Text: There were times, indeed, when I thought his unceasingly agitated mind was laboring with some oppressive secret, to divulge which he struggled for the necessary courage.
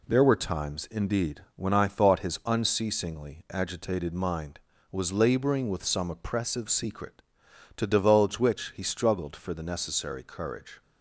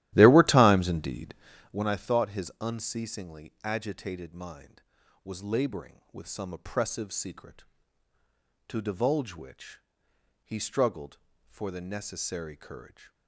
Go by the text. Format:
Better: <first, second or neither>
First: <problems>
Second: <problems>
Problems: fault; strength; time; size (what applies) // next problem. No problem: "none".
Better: first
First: none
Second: starts louder than the rest; strong; until 1.9 s; 14 dB // pauses between "which" and "he"; noticeable; at 9.7 s; 0.64 s long